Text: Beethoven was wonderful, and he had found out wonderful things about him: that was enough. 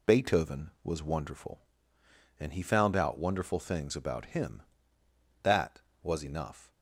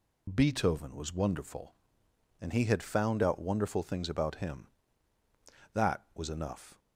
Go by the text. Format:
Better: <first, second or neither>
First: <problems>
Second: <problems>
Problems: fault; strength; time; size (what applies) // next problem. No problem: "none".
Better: second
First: skips "had"; at 2.6 s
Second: none